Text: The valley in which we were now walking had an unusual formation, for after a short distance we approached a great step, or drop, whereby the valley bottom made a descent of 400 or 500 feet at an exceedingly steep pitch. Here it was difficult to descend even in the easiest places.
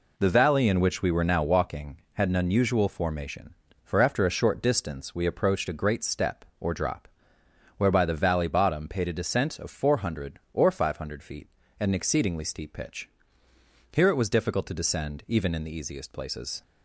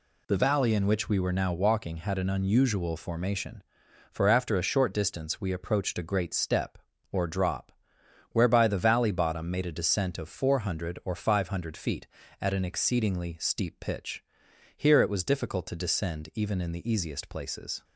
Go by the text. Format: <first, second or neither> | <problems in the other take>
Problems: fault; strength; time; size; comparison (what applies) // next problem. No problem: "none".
second | says "paid" for "made"; at 8.8 s